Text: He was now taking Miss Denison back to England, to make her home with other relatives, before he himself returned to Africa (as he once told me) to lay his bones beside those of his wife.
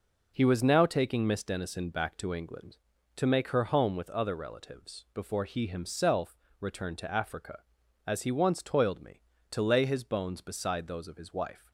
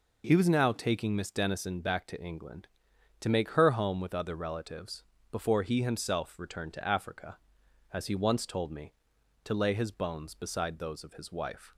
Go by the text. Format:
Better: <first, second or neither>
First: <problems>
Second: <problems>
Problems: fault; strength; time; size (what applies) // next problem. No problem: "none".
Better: second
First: pauses between "himself" and "returned"; slight; at 6.3 s; 0.22 s long // says "toiled" for "told"; at 8.6 s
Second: none